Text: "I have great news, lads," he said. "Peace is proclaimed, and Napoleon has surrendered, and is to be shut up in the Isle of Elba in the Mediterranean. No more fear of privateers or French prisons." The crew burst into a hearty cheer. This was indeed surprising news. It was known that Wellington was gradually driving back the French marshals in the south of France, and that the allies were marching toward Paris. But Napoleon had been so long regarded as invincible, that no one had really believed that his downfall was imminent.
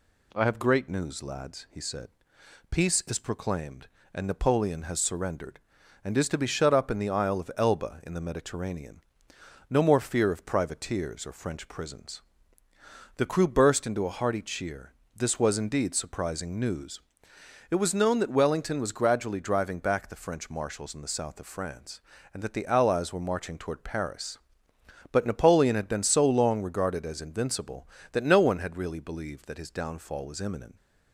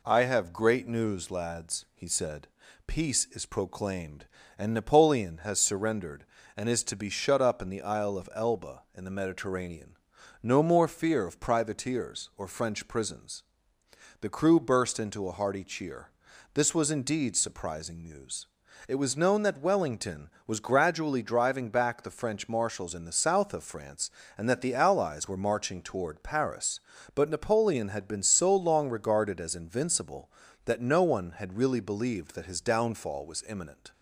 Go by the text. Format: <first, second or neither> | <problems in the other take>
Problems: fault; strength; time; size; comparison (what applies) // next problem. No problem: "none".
neither | none